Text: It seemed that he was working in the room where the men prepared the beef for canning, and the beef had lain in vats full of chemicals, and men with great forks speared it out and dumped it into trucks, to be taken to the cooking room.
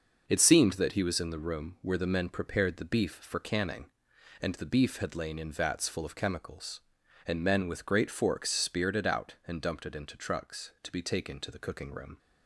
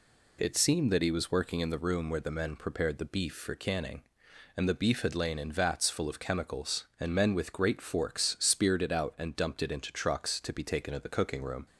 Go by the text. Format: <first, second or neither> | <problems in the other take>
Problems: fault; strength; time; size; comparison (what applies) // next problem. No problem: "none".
second | skips "working"; at 1.1 s